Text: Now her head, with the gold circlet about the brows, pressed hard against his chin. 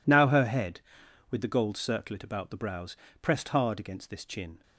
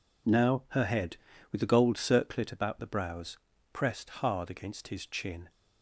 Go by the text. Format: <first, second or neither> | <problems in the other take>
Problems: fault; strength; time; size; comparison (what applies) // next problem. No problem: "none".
second | says "this" for "his"; at 4.0 s